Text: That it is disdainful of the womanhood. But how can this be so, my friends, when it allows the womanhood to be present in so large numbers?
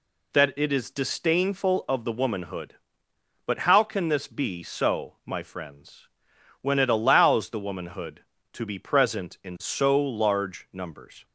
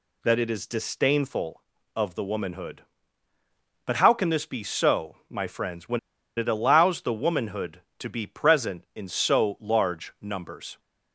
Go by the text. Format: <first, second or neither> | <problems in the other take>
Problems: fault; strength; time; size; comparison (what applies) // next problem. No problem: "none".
first | pauses between "when" and "it"; at 5.9 s; 0.37 s long